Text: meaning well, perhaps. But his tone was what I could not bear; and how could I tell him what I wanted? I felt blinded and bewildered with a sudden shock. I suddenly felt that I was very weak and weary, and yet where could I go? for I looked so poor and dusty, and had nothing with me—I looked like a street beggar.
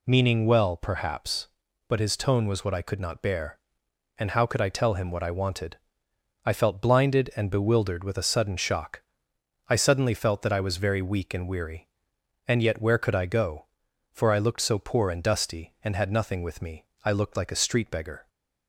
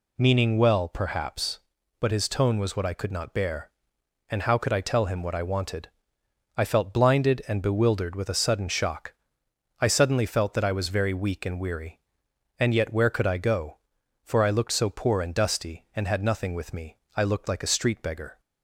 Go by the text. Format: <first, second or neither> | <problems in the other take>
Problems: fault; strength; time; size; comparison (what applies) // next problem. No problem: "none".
neither | none